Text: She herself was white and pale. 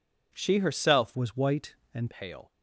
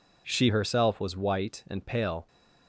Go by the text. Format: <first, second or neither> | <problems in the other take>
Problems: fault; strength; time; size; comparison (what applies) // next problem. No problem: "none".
second | changes voice from "was" to "and"; from 1.1 to 2.1 s; 1.0 s long